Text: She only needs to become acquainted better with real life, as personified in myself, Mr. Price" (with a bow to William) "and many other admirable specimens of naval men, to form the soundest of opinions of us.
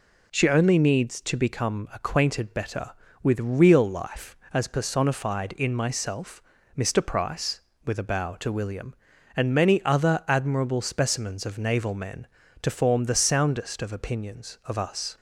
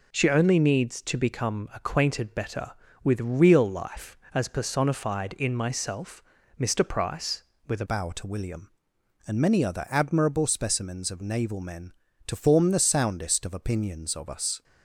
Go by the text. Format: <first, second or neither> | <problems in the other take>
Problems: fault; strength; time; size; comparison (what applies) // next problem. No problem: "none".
first | changes voice at "bow"; from 7.8 s on; 6.8 s long